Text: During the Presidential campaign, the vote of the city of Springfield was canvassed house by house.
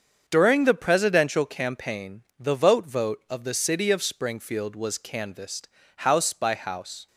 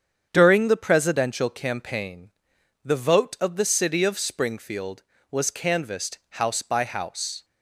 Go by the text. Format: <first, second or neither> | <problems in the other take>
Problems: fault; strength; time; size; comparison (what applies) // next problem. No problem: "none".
second | starts louder than the rest; until 1.2 s; 7 dB; strong in the second // says "vote" twice; at 2.8 s // pauses between "canvassed" and "house"; slight; at 5.6 s; 0.30 s long